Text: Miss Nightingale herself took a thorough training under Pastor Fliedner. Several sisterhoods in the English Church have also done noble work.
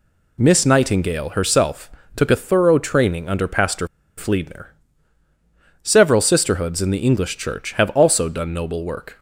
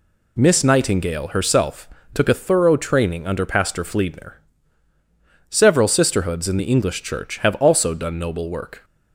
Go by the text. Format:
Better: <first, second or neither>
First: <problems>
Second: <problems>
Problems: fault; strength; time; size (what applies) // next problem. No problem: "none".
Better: second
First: pauses between "herself" and "took"; slight; at 1.9 s; 0.24 s long // pauses between "Pastor" and "Fliedner"; slight; at 3.8 s; 0.30 s long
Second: pauses between "herself" and "took"; slight; at 1.8 s; 0.24 s long